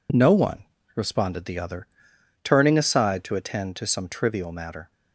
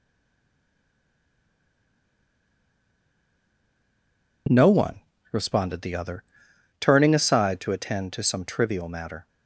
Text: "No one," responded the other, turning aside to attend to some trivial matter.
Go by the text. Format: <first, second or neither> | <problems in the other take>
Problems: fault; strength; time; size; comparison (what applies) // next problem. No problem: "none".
first | stays silent before the first word; strong; until 4.4 s; 4.4 s long